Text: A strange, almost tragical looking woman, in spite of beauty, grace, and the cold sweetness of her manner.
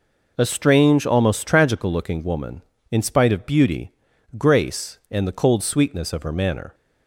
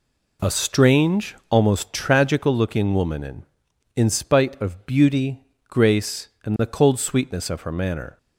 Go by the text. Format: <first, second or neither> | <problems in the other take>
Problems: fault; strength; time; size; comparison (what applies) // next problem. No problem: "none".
first | says "in" twice; at 3.9 s